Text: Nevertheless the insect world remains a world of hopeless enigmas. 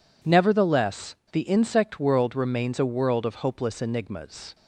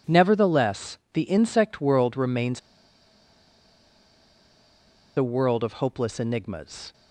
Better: first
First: pauses between "Nevertheless" and "the"; slight; at 1.1 s; 0.17 s long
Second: pauses between "Nevertheless" and "the"; slight; at 0.9 s; 0.16 s long // pauses between "remains" and "a"; strong; at 2.5 s; 2.5 s long

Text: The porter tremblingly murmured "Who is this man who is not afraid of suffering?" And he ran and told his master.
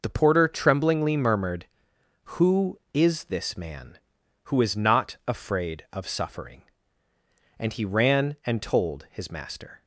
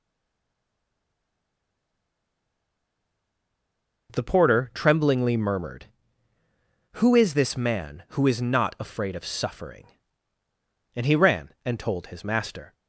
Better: first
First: none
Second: stays silent before the first word; strong; until 4.0 s; 4.0 s long

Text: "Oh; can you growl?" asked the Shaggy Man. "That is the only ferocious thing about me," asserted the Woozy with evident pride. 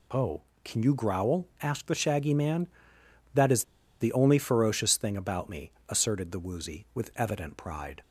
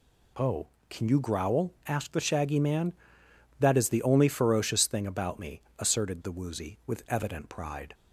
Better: second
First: pauses between "is" and "the"; at 3.6 s; 0.36 s long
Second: none

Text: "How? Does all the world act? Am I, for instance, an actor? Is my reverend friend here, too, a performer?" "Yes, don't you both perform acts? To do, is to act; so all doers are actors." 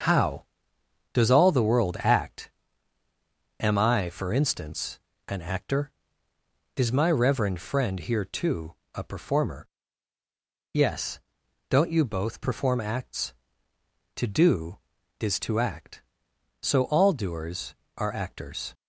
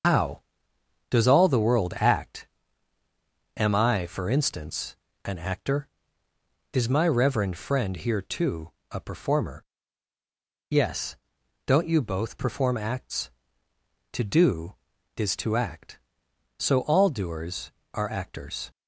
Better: first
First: starts louder than the rest; until 1.7 s; 6.5 dB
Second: loses the start of "How"; at 0.0 s; 75 ms // starts louder than the rest; until 1.7 s; 6.5 dB

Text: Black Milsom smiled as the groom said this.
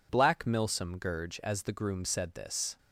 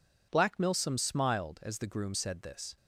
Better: second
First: says "gurge" for "smiled"; at 0.9 s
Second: none

